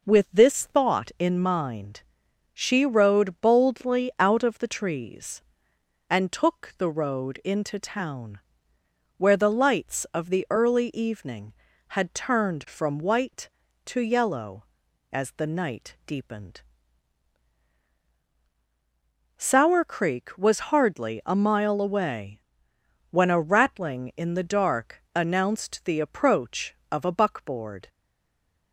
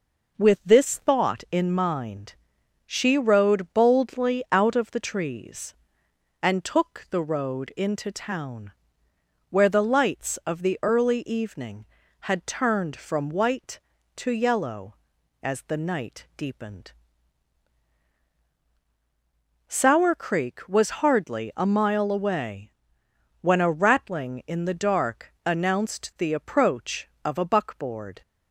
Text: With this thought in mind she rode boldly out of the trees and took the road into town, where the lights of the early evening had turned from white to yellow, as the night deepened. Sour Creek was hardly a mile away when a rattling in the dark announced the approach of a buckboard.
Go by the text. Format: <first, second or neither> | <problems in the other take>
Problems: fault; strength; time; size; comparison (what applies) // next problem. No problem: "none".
second | pauses between "mind" and "she"; noticeable; at 2.0 s; 0.50 s long; noticeable in the second // pauses between "away" and "when"; noticeable; at 22.4 s; 0.70 s long; noticeable in the second // stays silent after the last word; slight; from 27.8 s on; 0.9 s long